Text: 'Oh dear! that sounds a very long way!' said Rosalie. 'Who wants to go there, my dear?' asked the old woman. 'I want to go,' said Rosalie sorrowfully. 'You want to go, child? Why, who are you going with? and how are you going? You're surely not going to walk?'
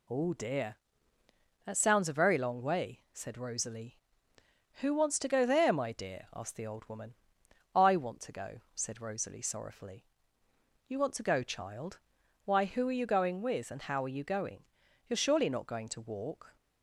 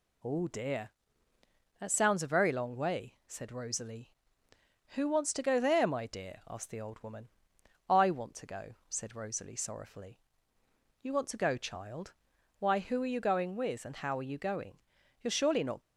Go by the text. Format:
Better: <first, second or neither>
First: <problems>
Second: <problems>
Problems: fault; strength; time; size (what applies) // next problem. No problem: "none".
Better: first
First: none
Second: stops before "going to walk"; at 15.8 s